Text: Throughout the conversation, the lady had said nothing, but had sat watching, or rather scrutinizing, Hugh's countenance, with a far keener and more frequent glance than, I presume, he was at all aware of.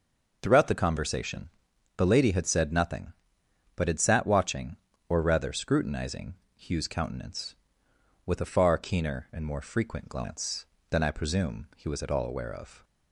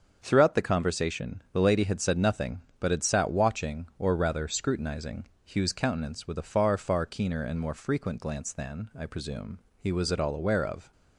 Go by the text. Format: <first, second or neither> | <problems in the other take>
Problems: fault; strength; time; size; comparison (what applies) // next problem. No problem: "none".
first | starts louder than the rest; until 1.2 s; 7 dB // says "far" twice; at 6.7 s